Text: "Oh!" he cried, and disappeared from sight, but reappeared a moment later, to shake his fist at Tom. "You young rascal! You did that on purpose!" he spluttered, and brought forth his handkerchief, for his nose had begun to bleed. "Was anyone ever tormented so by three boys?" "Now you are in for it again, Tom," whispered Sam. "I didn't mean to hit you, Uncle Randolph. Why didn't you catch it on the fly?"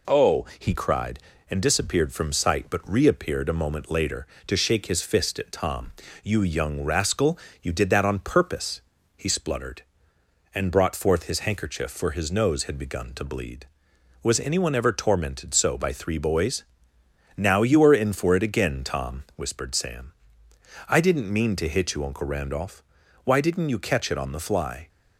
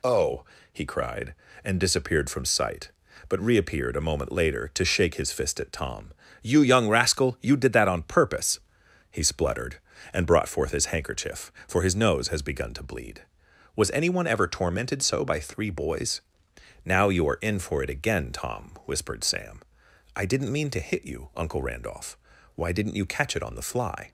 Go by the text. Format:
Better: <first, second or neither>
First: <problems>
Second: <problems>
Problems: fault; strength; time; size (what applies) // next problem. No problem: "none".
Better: first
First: none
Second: says "has" for "had"; at 12.2 s